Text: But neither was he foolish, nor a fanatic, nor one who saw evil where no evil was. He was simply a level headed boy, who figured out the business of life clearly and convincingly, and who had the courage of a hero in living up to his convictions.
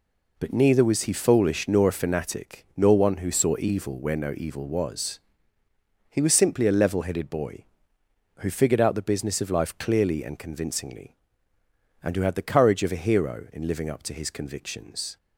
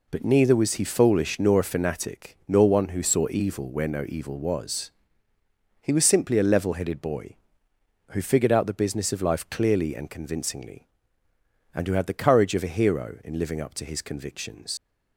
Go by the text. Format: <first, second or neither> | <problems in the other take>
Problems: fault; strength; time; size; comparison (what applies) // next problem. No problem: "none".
first | leaves "convictions" unfinished; at 14.7 s; 105 ms